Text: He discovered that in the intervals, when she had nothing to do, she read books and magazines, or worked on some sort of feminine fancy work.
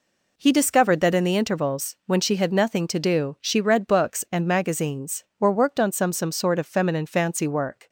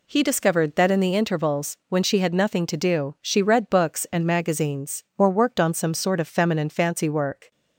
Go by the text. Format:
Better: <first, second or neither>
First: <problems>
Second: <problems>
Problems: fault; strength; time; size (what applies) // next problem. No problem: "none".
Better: second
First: says "some" twice; at 6.1 s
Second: none